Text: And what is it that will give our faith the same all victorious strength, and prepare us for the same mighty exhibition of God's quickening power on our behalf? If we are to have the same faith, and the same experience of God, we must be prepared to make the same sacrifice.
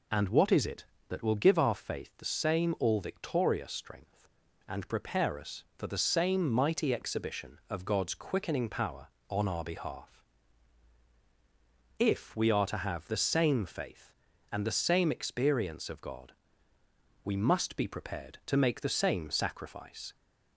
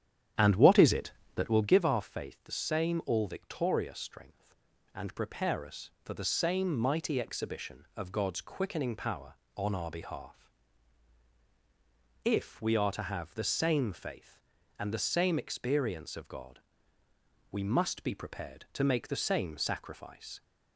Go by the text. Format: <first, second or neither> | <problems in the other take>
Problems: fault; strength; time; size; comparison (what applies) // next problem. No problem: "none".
first | starts louder than the rest; strong; until 1.8 s; 10 dB